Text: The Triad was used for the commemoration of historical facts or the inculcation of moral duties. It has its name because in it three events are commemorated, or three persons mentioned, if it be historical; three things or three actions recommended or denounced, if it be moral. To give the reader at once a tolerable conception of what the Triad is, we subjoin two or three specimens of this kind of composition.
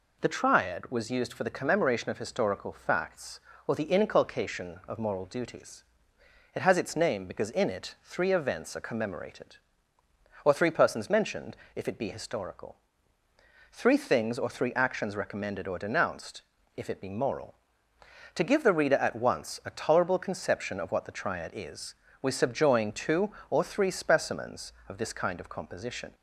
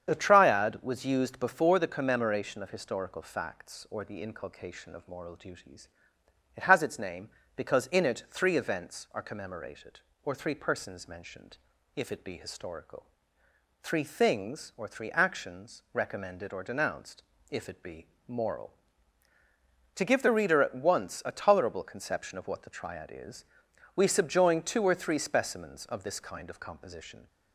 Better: first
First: none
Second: starts louder than the rest; strong; until 1.1 s; 8 dB // says "before" for "for"; at 1.3 s // pauses between "be" and "moral"; slight; at 18.0 s; 0.20 s long

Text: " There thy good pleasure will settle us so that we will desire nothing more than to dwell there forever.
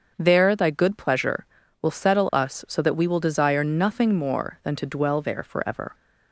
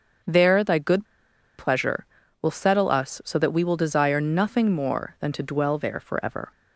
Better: first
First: starts louder than the rest; until 1.1 s; 6.5 dB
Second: starts louder than the rest; until 1.7 s; 6.5 dB // pauses between "good" and "pleasure"; noticeable; at 1.0 s; 0.52 s long

